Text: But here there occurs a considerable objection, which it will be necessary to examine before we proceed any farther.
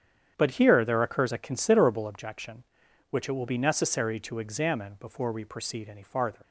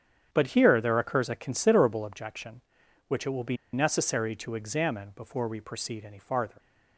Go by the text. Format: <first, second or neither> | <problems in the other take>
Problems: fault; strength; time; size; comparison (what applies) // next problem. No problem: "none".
first | starts louder than the rest; strong; until 1.3 s; 8.5 dB; strong in the first // pauses between "be" and "necessary"; slight; at 3.5 s; 0.16 s long